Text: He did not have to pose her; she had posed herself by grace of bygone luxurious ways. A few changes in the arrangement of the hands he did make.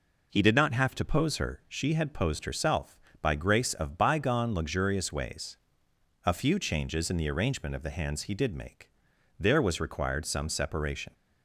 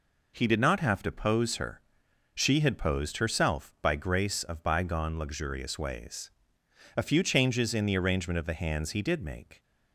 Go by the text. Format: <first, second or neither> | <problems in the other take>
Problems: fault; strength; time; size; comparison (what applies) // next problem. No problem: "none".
second | goes on to say "There was required some separation"; strong; from 9.4 s on; 1.7 s long